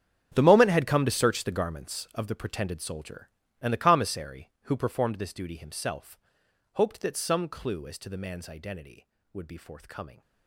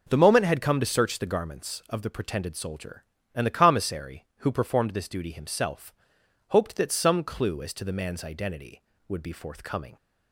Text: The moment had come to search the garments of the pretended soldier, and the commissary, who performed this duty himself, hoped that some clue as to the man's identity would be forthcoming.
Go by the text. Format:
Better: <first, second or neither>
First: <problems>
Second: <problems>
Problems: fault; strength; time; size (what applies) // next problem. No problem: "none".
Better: second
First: gets quieter; strong; throughout; 16.5 dB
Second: none